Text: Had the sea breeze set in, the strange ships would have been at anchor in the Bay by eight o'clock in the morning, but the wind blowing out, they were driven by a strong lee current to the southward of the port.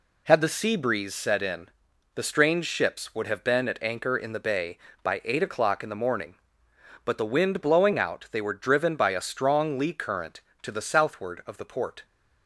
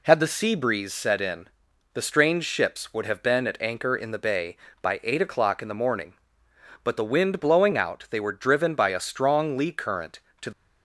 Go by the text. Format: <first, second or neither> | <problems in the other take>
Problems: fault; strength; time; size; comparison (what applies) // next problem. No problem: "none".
first | stops before "the southward of the port"; at 10.5 s